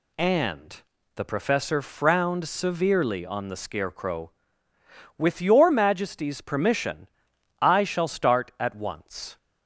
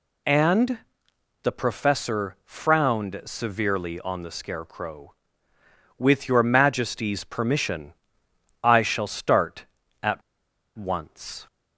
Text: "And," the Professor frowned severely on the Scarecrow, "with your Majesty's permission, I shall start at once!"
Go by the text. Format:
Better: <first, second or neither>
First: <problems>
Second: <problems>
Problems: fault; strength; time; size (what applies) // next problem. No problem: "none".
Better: first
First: none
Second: pauses between "at" and "once"; noticeable; at 10.2 s; 0.55 s long